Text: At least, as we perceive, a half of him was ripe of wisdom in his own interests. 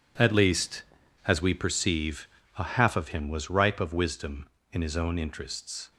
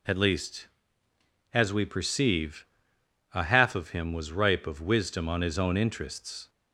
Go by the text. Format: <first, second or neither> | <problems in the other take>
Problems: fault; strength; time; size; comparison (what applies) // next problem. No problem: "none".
first | says "on" for "in"; at 5.2 s